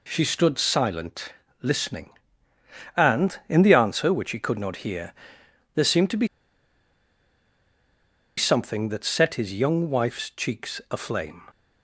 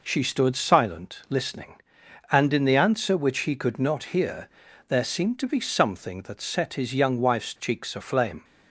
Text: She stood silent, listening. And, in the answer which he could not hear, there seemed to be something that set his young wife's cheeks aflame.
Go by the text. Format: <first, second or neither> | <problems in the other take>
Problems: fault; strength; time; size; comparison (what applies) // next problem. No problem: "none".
second | pauses between "be" and "something"; strong; at 6.2 s; 2.1 s long